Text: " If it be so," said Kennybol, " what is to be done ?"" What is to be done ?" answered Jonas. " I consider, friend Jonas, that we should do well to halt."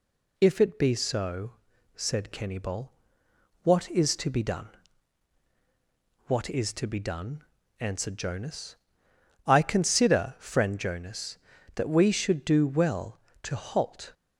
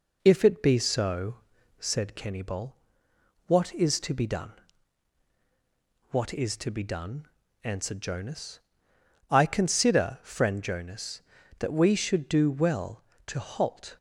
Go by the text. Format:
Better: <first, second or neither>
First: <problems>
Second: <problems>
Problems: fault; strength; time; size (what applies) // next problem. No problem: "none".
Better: first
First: none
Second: starts louder than the rest; noticeable; until 2.1 s; 5.5 dB